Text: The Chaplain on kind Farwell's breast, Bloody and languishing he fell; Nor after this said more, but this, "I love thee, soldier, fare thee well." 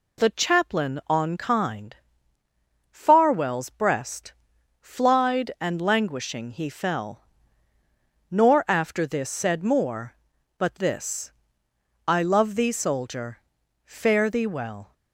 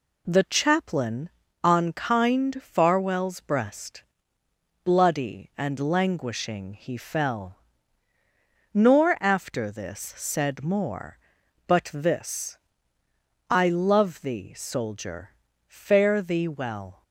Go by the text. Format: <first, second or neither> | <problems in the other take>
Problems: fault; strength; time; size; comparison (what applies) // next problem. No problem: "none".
second | pauses between "kind" and "Farwell's"; noticeable; at 1.9 s; 0.96 s long // says "Flied" for "Bloody"; at 4.8 s